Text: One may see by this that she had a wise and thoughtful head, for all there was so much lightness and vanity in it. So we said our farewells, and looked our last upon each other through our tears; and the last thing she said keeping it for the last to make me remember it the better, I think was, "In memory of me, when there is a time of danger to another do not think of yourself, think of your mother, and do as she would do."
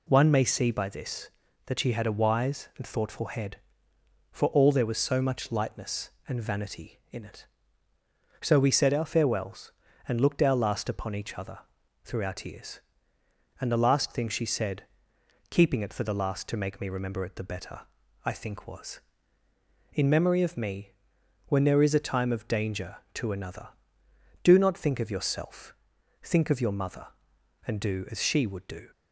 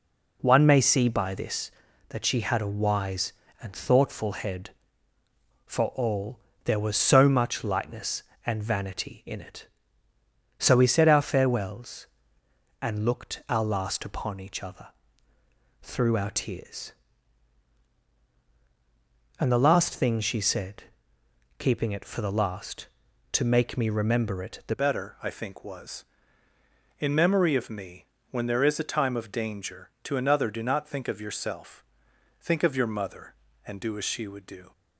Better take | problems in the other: first | pauses between "all" and "there"; slight; at 6.3 s; 0.26 s long // pauses between "other" and "through"; noticeable; at 14.8 s; 0.94 s long; noticeable in the first // pauses between "said" and "keeping"; noticeable; at 20.8 s; 0.74 s long; noticeable in the first // changes voice at "better"; from 24.7 s on; 10.0 s long

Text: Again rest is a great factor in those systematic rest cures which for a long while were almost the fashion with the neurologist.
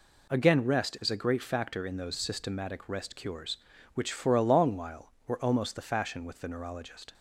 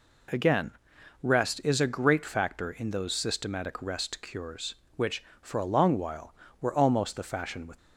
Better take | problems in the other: first | pauses between "Again" and "rest"; noticeable; at 0.7 s; 0.52 s long // stops before "the neurologist"; at 7.7 s

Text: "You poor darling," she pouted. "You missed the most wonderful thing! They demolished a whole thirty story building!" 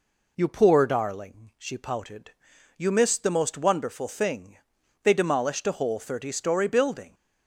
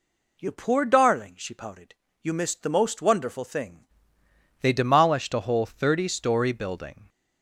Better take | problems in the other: first | changes voice at "They"; from 4.6 s on; 2.4 s long

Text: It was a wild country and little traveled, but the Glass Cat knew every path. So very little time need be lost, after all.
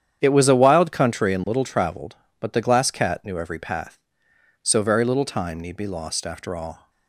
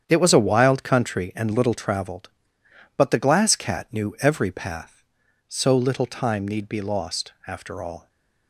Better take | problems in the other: first | starts louder than the rest; strong; until 1.0 s; 8.5 dB; strong in the first // skips "very"; at 5.7 s

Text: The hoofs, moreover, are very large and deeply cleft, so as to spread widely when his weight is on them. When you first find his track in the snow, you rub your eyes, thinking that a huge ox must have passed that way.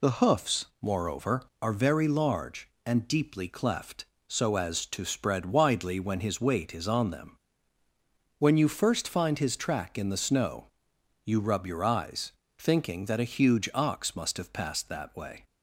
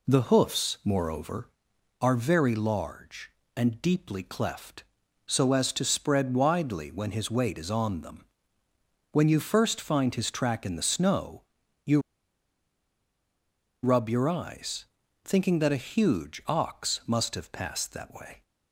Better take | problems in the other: first | pauses between "you" and "rub"; strong; at 12.0 s; 1.8 s long

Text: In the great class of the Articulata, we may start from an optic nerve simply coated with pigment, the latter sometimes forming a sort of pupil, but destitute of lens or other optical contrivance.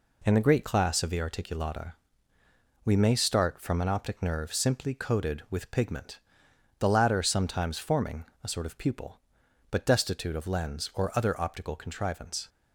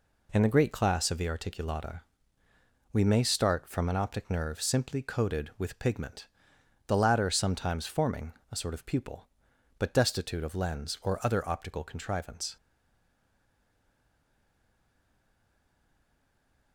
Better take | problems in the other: first | pauses between "forming" and "a"; slight; at 8.3 s; 0.20 s long; slight in the first // stays silent after the last word; strong; from 12.5 s on; 4.2 s long

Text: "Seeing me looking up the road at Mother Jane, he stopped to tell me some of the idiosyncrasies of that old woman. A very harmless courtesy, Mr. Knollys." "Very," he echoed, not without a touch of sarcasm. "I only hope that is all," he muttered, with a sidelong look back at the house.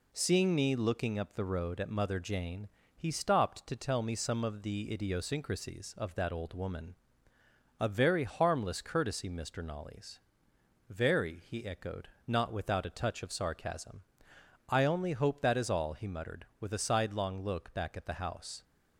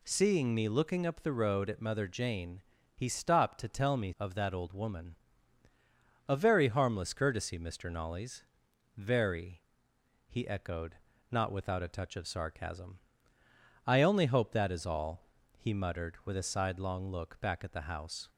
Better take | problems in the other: first | skips "some of the idiosyncrasies"; at 4.1 s

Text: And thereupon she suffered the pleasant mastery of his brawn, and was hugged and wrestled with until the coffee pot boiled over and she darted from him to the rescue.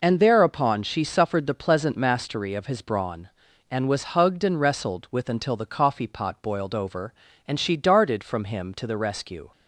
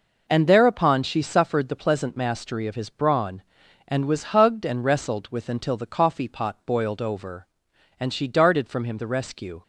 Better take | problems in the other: first | skips "to"; at 8.9 s

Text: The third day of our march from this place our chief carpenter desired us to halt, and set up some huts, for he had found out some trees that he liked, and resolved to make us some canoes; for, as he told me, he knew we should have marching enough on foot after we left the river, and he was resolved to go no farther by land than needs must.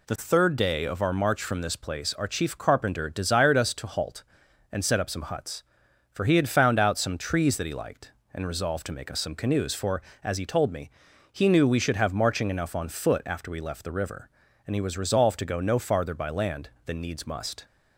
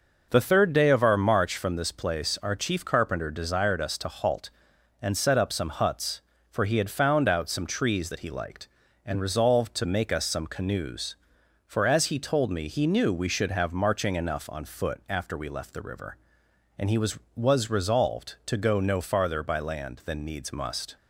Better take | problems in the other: first | says "was" twice; at 17.3 s

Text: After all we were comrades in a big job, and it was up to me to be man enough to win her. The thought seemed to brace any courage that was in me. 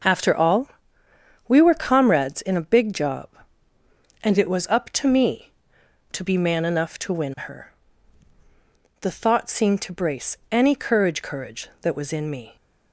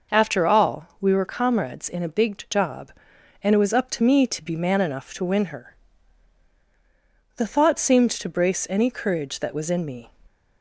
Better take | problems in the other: second | starts louder than the rest; until 1.8 s; 6 dB // pauses between "all" and "we"; noticeable; at 0.6 s; 0.80 s long // says "courage" twice; at 11.2 s

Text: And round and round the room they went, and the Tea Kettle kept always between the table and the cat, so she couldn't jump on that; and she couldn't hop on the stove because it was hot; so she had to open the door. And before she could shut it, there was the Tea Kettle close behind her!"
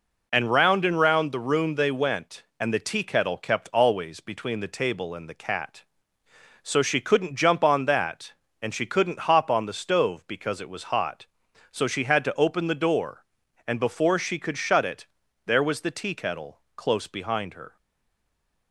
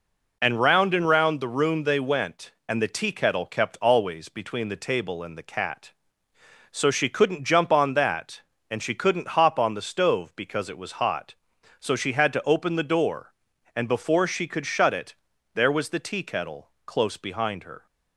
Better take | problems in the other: second | pauses between "Kettle" and "close"; slight; at 16.5 s; 0.16 s long; slight in the second // stays silent after the last word; from 17.7 s on; 1.0 s long

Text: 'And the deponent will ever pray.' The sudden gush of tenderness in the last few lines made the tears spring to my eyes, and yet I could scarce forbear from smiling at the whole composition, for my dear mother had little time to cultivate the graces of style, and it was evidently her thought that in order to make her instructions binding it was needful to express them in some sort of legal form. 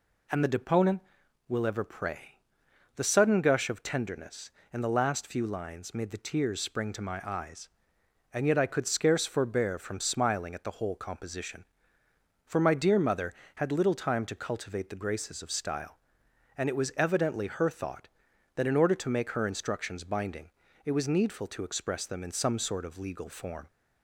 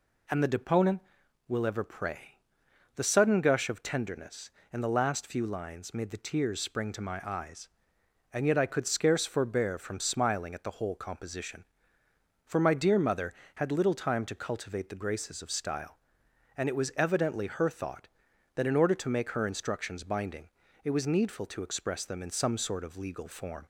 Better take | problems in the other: neither | pauses between "binding" and "it"; slight; the same in both

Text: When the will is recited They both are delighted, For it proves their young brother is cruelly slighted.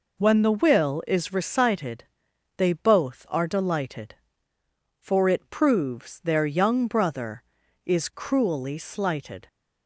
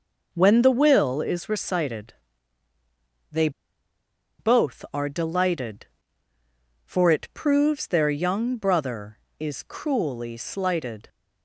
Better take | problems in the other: first | pauses between "recited" and "They"; at 2.1 s; 1.1 s long; noticeable in the first // pauses between "They" and "both"; noticeable; at 3.4 s; 0.89 s long

